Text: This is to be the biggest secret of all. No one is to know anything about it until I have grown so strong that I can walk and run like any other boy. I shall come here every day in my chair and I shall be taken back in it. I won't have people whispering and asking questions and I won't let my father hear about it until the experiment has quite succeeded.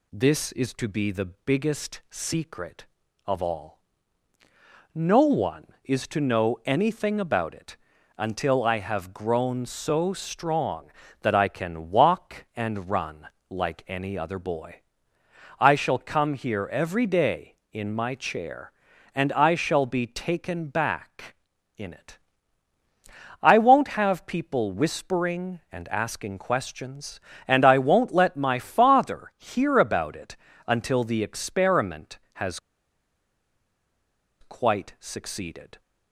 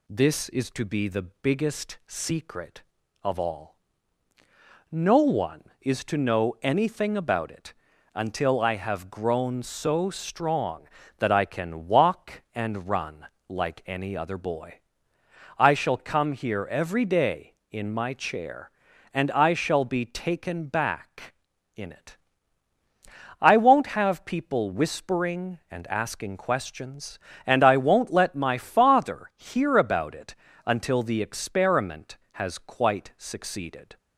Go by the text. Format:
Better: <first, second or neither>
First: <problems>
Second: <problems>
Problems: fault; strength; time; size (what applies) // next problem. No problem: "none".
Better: second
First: pauses between "it" and "until"; at 7.7 s; 0.40 s long // pauses between "run" and "like"; slight; at 13.2 s; 0.22 s long // pauses between "it" and "until"; slight; at 30.3 s; 0.30 s long // pauses between "has" and "quite"; strong; at 32.5 s; 1.8 s long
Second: pauses between "it" and "until"; at 7.7 s; 0.40 s long // pauses between "run" and "like"; slight; at 13.2 s; 0.22 s long // pauses between "it" and "until"; slight; at 30.3 s; 0.30 s long